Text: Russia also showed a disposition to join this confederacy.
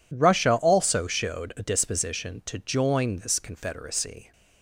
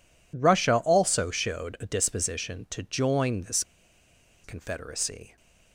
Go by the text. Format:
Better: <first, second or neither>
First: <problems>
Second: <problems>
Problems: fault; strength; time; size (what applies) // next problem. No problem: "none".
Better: first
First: none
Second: pauses between "this" and "confederacy"; noticeable; at 3.6 s; 0.81 s long